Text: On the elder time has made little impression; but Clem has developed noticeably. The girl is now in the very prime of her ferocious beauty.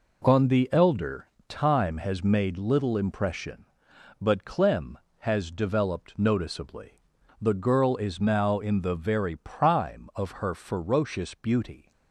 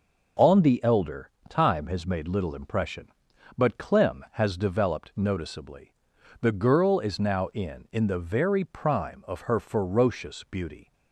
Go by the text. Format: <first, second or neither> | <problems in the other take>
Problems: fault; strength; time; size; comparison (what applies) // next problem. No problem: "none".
first | starts louder than the rest; noticeable; until 1.6 s; 6 dB // pauses between "elder" and "time"; slight; at 1.2 s; 0.20 s long; slight in the first // says "in" twice; at 7.9 s